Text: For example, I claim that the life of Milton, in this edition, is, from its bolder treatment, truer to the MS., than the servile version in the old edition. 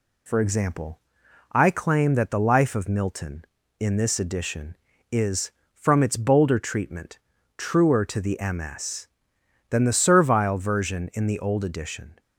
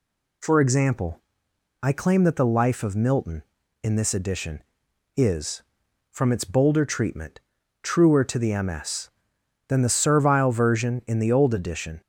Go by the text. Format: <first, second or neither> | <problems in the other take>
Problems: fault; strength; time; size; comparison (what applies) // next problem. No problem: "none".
neither | none